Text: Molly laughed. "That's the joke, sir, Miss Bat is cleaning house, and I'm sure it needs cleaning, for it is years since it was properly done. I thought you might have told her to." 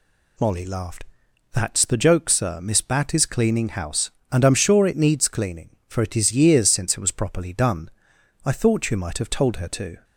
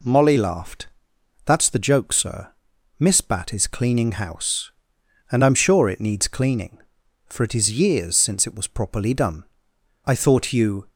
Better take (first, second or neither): first